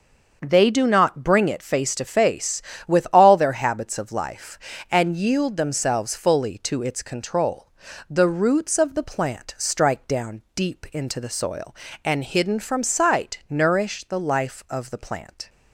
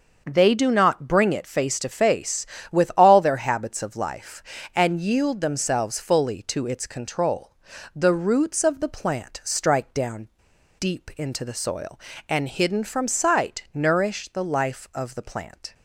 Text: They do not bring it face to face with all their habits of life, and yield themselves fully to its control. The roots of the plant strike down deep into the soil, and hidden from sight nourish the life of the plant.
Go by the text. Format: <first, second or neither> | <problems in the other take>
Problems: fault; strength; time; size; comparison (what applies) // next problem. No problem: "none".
first | starts louder than the rest; until 1.2 s; 6 dB; also in the first // pauses between "down" and "deep"; noticeable; at 10.2 s; 0.52 s long